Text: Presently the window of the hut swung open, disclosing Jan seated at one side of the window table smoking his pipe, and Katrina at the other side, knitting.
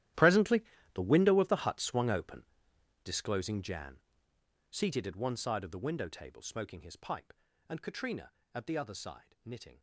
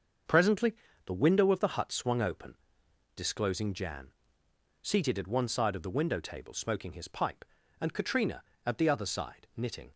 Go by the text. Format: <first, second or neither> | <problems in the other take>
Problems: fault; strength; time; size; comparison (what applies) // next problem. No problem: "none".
second | gets quieter; strong; throughout; 18 dB // starts louder than the rest; strong; until 1.5 s; 13 dB; also in the second // pauses between "Presently" and "the"; slight; at 0.6 s; 0.32 s long; slight in the second // pauses between "Jan" and "seated"; noticeable; at 3.9 s; 0.72 s long; noticeable in the second